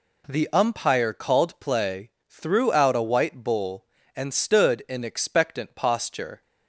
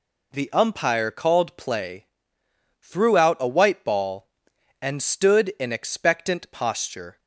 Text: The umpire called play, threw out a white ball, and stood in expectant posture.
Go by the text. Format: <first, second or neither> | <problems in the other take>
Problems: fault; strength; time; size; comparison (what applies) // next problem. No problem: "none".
second | says "bull" for "ball"; at 3.4 s